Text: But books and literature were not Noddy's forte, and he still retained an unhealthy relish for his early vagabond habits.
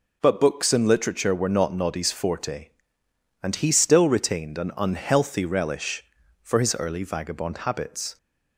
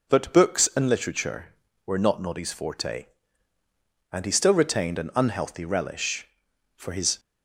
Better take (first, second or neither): first